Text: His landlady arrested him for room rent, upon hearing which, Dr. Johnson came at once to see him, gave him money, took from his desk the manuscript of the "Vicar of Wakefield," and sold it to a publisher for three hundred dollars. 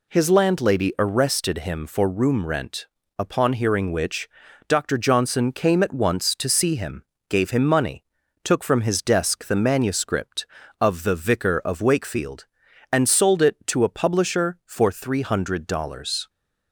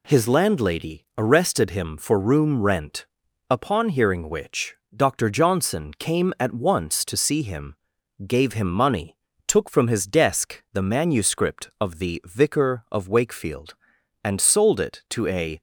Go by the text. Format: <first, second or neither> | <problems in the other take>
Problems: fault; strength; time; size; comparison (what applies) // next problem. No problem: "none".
first | stops before "publisher for three hundred dollars"; at 15.5 s